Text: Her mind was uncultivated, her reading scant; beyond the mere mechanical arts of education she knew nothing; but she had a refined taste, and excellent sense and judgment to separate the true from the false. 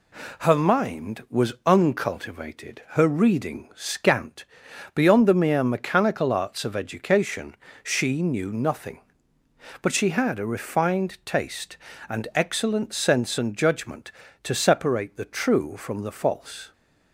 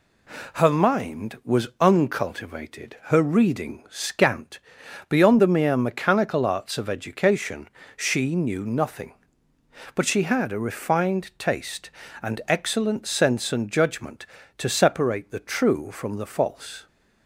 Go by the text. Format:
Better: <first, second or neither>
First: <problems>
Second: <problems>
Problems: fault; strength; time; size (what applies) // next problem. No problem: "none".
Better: neither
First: pauses between "education" and "she"; slight; at 7.5 s; 0.26 s long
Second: pauses between "education" and "she"; slight; at 7.6 s; 0.26 s long